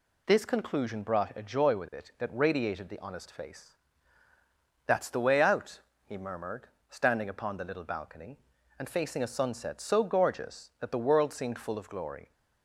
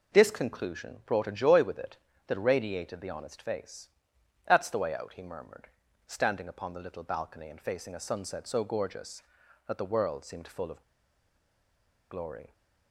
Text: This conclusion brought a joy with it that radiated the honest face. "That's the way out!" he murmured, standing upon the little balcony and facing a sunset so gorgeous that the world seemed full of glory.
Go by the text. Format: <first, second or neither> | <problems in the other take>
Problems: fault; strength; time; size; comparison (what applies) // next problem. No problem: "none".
first | pauses between "of" and "glory"; strong; at 10.8 s; 1.2 s long